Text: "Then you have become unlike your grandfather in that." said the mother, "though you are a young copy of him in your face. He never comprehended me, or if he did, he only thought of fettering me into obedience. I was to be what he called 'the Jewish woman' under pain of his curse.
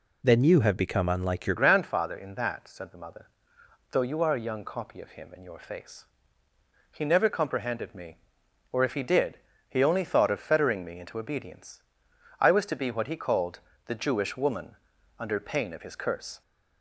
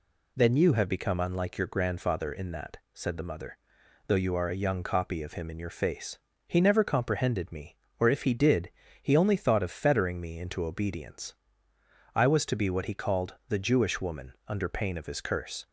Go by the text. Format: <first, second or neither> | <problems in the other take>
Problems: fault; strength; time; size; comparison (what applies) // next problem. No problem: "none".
second | changes voice at "grandfather"; from 1.5 s on; 14.9 s long // pauses between "called" and "the"; slight; at 13.5 s; 0.28 s long; slight in the second // pauses between "woman" and "under"; at 14.7 s; 0.42 s long; slight in the second